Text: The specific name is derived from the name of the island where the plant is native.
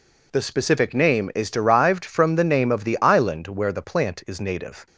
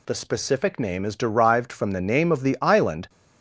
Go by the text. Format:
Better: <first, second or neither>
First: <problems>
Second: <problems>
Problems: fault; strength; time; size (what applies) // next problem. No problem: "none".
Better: first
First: none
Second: stops before "where the plant is native"; at 3.0 s